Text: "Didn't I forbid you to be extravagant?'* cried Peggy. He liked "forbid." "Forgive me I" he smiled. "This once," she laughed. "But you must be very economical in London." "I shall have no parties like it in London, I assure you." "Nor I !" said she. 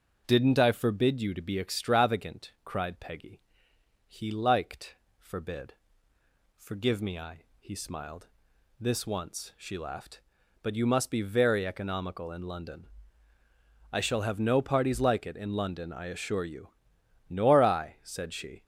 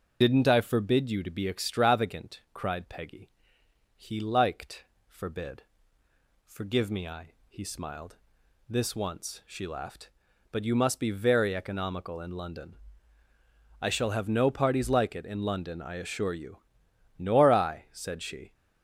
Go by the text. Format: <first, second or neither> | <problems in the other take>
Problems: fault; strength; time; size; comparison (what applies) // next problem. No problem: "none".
first | loses the start of "Didn't"; at 0.2 s; 50 ms // starts louder than the rest; until 1.2 s; 6.5 dB; also in the first // pauses between "liked" and "forbid"; slight; at 4.8 s; 0.22 s long; slight in the first // pauses between "I" and "he"; slight; at 7.3 s; 0.16 s long; slight in the first